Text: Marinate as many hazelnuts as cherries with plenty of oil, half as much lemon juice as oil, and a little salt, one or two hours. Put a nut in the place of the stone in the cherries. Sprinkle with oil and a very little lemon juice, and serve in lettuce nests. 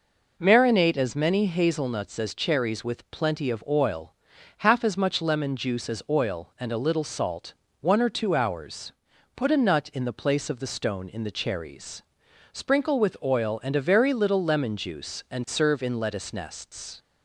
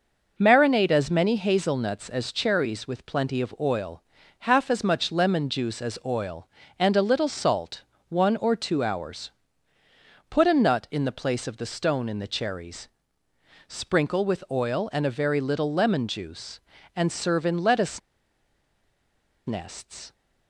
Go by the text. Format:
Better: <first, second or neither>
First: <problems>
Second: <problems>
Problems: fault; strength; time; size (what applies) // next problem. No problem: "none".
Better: first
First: none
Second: pauses between "lettuce" and "nests"; strong; at 17.9 s; 1.4 s long